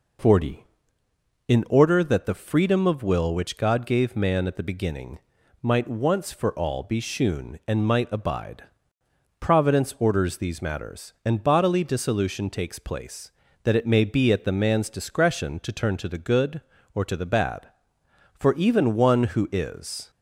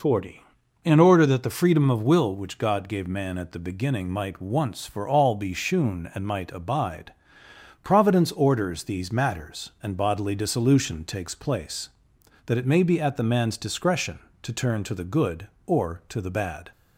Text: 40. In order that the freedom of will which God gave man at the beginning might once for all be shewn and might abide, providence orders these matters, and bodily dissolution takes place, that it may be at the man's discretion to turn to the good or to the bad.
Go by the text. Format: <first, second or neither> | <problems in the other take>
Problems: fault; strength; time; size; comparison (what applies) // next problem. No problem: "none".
second | pauses between "beginning" and "might"; at 5.1 s; 0.44 s long // goes on to say "For even one who is"; strong; from 18.3 s on; 1.7 s long